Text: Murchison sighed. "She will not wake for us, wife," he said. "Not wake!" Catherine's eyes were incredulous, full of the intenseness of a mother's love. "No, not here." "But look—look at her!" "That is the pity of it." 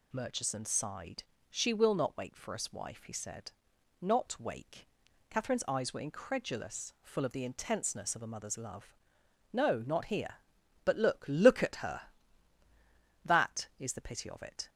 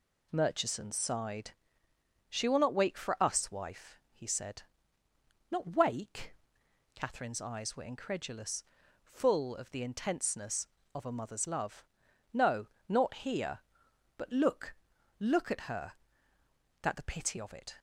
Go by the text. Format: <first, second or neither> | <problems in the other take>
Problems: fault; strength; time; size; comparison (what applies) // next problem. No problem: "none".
first | skips "is"; at 16.9 s